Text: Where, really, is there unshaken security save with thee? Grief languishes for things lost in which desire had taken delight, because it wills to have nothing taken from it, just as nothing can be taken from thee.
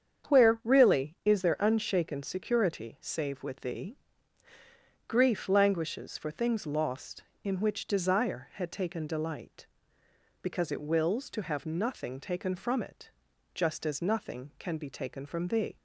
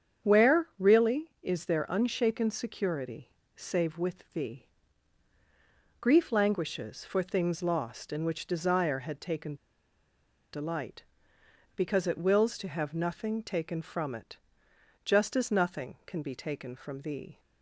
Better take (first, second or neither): first